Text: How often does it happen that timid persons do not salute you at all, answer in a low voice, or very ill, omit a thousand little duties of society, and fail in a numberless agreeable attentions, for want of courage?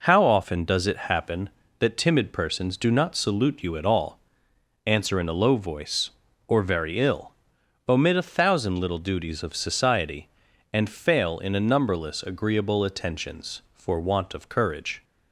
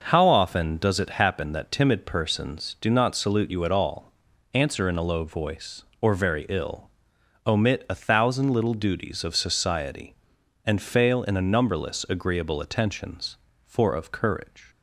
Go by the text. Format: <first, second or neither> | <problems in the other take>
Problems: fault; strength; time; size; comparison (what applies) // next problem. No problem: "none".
first | skips "want"; at 13.9 s